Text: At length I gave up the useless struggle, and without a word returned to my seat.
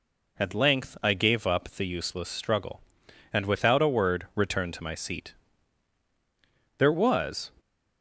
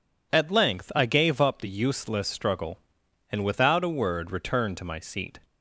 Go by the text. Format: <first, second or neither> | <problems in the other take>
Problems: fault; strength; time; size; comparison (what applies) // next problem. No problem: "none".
second | goes on to say "There was"; noticeable; from 6.7 s on; 0.74 s long